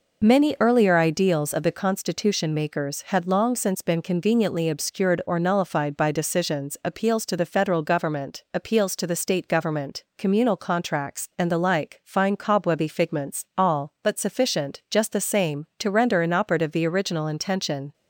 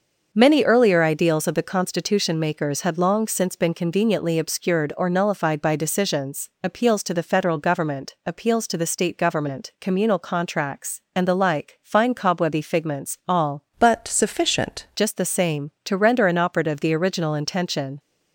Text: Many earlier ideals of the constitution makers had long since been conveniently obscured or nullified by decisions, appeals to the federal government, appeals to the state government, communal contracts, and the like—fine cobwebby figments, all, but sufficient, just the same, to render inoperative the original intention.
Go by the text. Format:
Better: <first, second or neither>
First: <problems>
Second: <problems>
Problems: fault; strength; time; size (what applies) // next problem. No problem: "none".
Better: first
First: none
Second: starts louder than the rest; until 1.3 s; 6 dB // changes voice from "but" to "sufficient"; from 13.7 to 14.8 s; 1.1 s long